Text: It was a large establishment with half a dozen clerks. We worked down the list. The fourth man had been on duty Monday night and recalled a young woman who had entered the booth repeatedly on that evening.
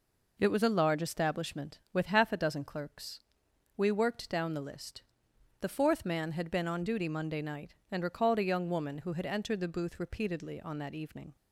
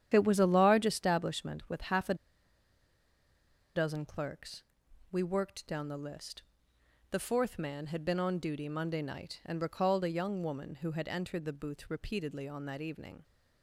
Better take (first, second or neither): first